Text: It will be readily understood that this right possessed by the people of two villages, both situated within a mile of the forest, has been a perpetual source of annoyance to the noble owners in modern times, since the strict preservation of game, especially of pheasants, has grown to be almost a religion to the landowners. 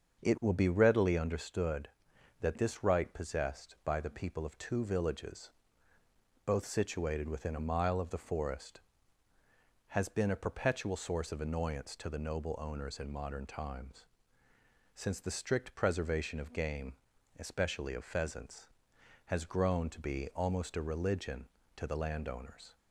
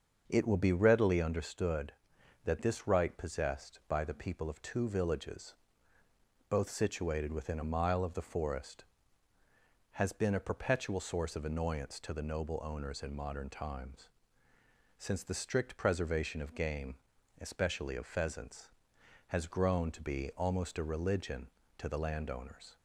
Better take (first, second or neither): neither